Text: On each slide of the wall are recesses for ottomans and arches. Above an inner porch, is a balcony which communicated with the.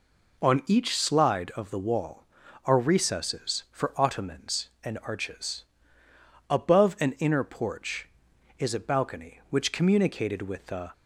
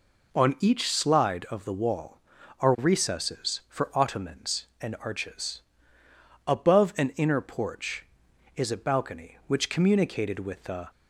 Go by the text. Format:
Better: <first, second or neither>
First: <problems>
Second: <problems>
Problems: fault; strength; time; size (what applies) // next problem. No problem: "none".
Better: neither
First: none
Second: none